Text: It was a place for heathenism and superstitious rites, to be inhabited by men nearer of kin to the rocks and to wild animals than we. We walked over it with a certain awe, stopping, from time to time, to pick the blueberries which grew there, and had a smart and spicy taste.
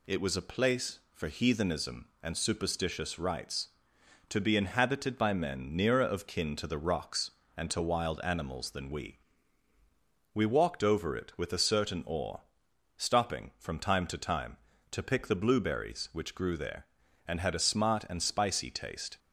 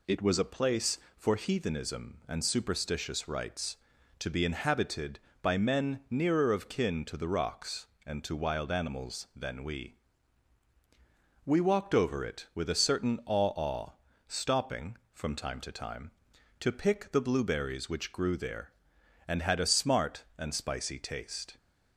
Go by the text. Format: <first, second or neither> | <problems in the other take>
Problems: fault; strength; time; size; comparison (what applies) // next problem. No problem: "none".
first | says "awe" twice; at 13.5 s